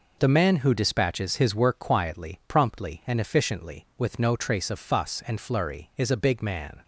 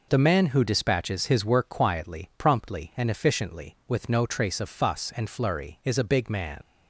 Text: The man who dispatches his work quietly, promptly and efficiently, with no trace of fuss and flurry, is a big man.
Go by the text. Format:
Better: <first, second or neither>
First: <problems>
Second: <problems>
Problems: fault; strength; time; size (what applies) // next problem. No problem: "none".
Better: first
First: none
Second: leaves "man" unfinished; at 6.6 s; 90 ms